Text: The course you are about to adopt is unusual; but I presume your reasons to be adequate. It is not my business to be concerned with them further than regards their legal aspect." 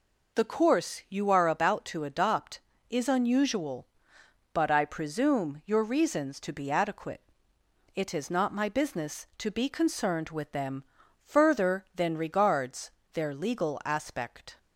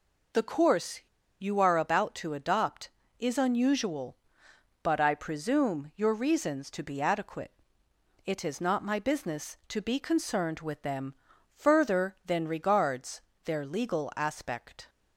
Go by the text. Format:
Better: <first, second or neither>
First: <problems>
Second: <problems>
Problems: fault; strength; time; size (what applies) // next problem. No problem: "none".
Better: first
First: pauses between "them" and "further"; at 10.8 s; 0.38 s long // pauses between "regards" and "their"; slight; at 12.9 s; 0.23 s long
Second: pauses between "course" and "you"; at 0.9 s; 0.40 s long // pauses between "them" and "further"; at 11.1 s; 0.38 s long // pauses between "regards" and "their"; slight; at 13.2 s; 0.24 s long